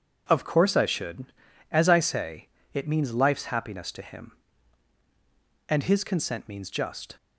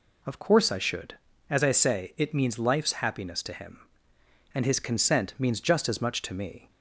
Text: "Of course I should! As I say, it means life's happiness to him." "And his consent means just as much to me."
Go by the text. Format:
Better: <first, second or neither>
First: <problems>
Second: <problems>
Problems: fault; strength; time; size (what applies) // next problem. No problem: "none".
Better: second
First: stops before "as much to me"; at 7.1 s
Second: none